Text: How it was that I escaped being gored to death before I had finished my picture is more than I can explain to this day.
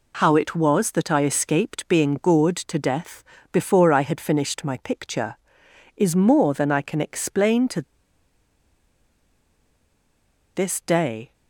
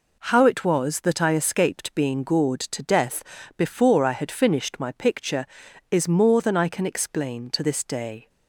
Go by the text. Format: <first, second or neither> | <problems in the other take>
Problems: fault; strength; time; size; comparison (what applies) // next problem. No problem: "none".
second | pauses between "death" and "before"; slight; at 3.2 s; 0.30 s long; slight in the second // pauses between "to" and "this"; strong; at 7.8 s; 2.7 s long